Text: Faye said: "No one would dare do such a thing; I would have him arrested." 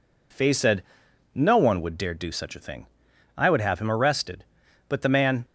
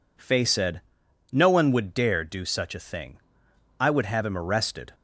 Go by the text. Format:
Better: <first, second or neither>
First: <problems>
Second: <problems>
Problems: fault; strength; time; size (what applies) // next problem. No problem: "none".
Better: second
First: goes on to say "But the man"; from 4.8 s on; 0.58 s long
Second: none